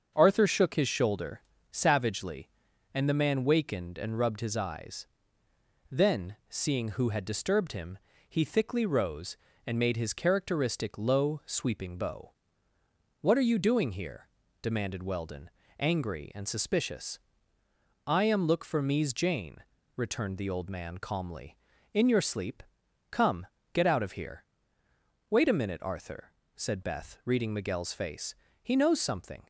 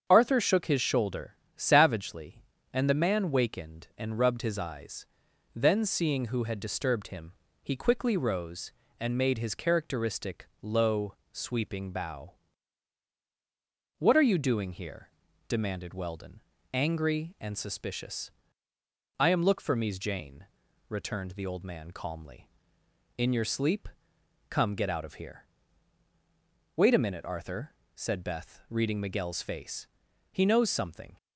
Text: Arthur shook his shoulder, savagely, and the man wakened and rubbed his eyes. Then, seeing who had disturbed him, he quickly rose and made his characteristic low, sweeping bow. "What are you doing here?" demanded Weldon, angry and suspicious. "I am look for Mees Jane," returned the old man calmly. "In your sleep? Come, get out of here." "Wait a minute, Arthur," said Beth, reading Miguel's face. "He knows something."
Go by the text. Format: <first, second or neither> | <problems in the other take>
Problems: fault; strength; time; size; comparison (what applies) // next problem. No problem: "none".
second | starts louder than the rest; until 1.1 s; 6.5 dB; strong in the second // says "thickly" for "quickly"; at 8.4 s